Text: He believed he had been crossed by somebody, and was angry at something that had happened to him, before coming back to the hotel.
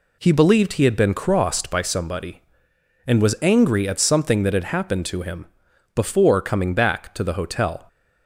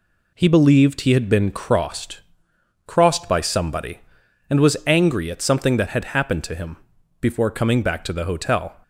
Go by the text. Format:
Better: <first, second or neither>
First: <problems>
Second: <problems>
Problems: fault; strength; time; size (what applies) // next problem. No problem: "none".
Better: first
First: none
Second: says "crossed" twice; at 2.8 s